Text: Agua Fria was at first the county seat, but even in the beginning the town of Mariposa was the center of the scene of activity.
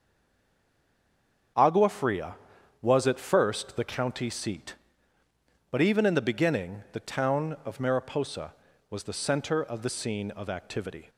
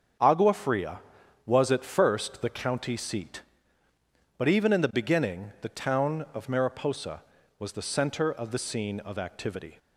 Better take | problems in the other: second | stays silent before the first word; noticeable; until 1.5 s; 1.5 s long // starts louder than the rest; strong; until 3.0 s; 7.5 dB; strong in the second

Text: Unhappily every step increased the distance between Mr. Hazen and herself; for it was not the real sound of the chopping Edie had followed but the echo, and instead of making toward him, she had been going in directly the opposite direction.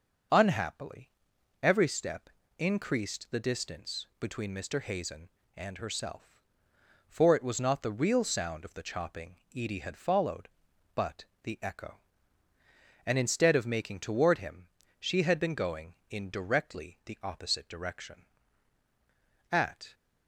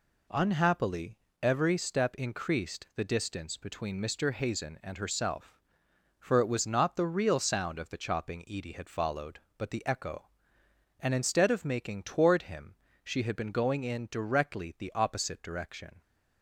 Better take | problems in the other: second | starts louder than the rest; noticeable; until 1.8 s; 6 dB // pauses between "Unhappily" and "every"; noticeable; at 1.1 s; 0.50 s long; slight in the second // pauses between "step" and "increased"; slight; at 2.2 s; 0.28 s long // pauses between "chopping" and "Edie"; slight; at 9.3 s; 0.20 s long // pauses between "but" and "the"; slight; at 11.2 s; 0.18 s long // goes on to say "At"; slight; from 19.5 s on; 0.42 s long

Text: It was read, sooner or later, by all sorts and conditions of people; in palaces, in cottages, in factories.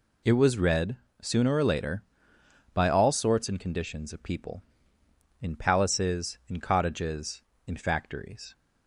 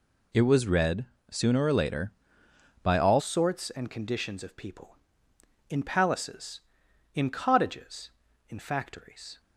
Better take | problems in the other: first | changes voice at "sorts"; from 3.1 s on; 6.3 s long

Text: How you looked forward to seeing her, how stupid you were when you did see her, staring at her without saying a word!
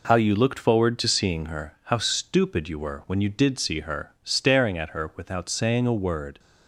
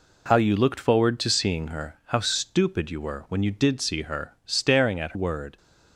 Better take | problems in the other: first | skips "her without saying a"; at 5.1 s

